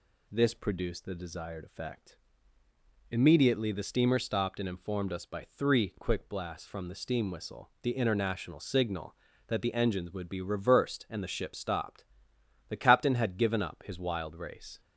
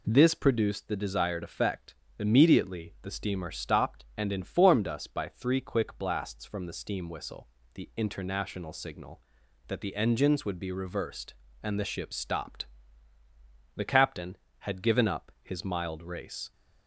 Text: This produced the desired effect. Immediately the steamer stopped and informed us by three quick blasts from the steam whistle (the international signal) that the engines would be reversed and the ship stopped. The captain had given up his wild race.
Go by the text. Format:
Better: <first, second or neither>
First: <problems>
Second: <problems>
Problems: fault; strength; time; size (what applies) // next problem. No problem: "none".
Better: first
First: none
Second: says "mild" for "wild"; at 15.6 s